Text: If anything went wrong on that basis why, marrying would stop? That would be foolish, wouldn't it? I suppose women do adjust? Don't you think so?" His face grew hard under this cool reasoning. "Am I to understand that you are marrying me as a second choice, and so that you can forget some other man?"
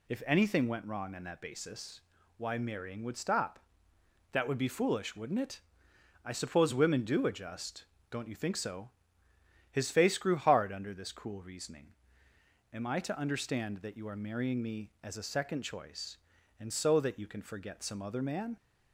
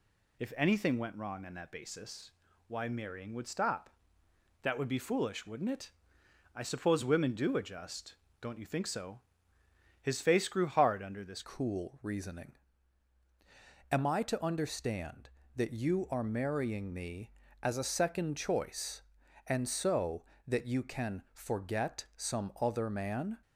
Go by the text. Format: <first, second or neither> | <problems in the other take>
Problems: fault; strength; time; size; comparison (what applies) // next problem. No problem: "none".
first | pauses between "basis" and "why"; slight; at 2.3 s; 0.36 s long; slight in the first // changes voice at "cool"; from 11.4 s on; 11.9 s long